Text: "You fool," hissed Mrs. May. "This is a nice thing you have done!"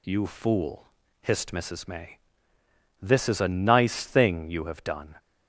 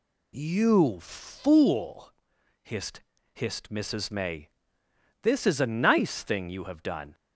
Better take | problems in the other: first | says "hissed" twice; at 3.3 s

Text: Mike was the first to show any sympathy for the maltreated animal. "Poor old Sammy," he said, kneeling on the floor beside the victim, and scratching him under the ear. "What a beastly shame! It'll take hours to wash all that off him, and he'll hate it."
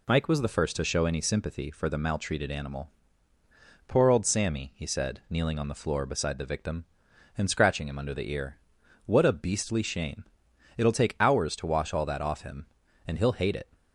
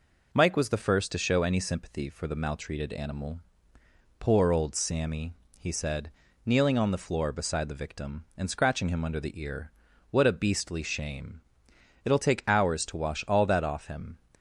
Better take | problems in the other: first | stops before "and he'll hate it"; at 14.3 s

